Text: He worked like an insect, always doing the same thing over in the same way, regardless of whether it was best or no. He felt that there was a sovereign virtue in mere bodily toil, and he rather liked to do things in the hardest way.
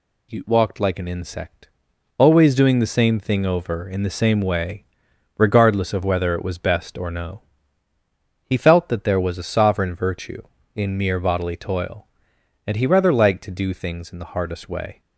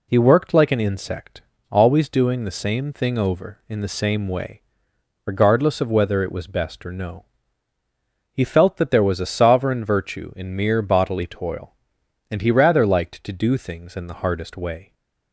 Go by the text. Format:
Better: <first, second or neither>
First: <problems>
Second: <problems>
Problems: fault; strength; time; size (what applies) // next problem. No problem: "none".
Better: second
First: says "walked" for "worked"; at 0.4 s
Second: none